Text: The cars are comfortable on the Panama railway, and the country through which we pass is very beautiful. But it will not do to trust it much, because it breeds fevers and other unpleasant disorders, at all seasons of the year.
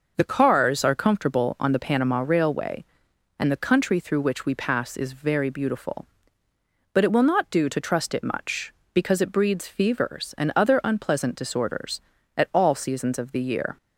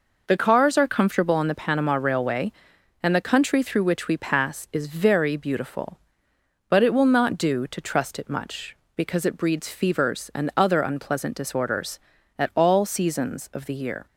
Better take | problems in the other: neither | none

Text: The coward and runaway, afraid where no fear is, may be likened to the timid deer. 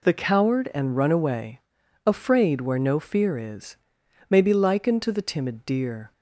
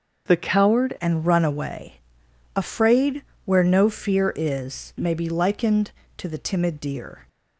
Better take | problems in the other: first | starts louder than the rest; until 1.3 s; 6.5 dB // changes voice at "and"; from 0.9 s on; 6.3 s long // pauses between "afraid" and "where"; slight; at 3.2 s; 0.24 s long

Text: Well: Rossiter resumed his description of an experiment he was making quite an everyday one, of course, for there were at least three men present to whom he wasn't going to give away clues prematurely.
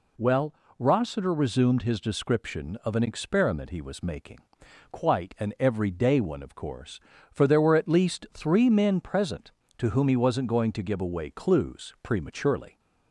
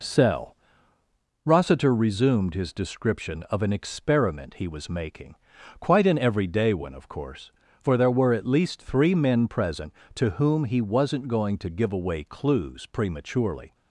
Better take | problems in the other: first | says "Cell" for "Well"; at 0.0 s // pauses between "making" and "quite"; at 5.3 s; 0.44 s long; noticeable in the first

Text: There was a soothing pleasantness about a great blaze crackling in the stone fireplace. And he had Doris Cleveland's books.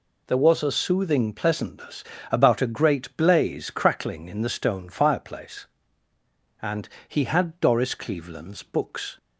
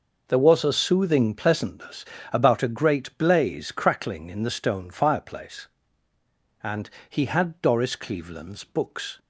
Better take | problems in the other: first | starts louder than the rest; noticeable; until 1.7 s; 5.5 dB // pauses between "pleasantness" and "about"; slight; at 2.0 s; 0.28 s long; slight in the first // pauses between "And" and "he"; slight; at 6.8 s; 0.22 s long; slight in the first

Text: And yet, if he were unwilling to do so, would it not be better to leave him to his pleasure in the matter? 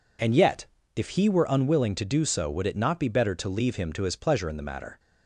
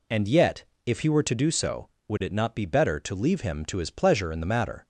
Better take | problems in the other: first | skips "unwilling"; at 1.2 s

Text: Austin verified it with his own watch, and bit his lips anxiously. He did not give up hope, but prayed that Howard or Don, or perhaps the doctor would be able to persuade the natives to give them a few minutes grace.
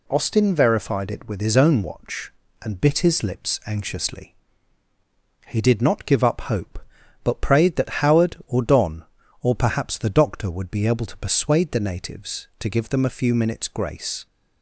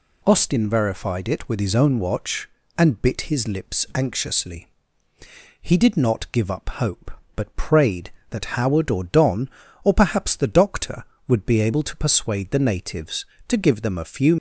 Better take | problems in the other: first | stops before "minutes grace"; at 14.3 s

